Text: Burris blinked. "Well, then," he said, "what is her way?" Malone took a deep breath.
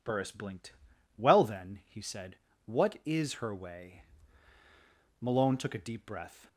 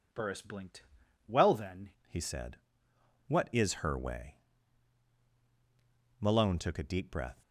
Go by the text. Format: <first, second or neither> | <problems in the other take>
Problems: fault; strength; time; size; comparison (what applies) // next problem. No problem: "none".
first | changes voice at "he"; from 2.0 s on; 5.4 s long